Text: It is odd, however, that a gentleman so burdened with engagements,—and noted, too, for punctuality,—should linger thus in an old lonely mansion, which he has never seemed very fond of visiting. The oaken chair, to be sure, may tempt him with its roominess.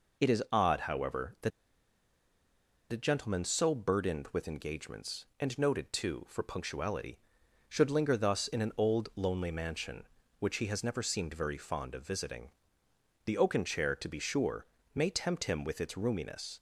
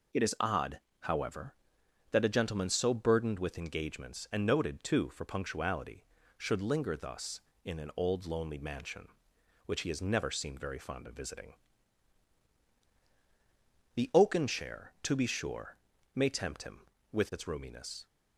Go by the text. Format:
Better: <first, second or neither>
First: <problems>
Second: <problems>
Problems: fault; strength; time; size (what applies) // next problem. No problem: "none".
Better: second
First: pauses between "that" and "a"; strong; at 1.5 s; 1.4 s long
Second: none